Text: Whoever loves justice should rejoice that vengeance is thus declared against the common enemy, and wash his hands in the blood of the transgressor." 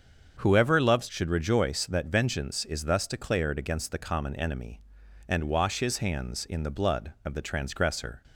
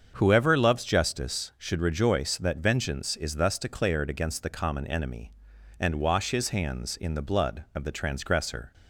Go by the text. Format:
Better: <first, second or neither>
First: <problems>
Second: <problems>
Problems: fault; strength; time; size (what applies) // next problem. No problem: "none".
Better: second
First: starts louder than the rest; until 1.4 s; 7 dB // skips "justice"; at 1.0 s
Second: starts louder than the rest; strong; until 1.1 s; 7 dB